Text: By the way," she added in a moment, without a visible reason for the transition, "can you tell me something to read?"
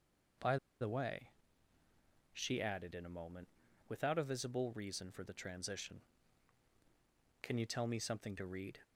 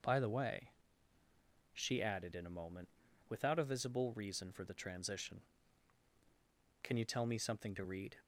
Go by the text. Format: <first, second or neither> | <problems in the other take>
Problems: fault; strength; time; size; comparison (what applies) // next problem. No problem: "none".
second | pauses between "By" and "the"; slight; at 0.5 s; 0.24 s long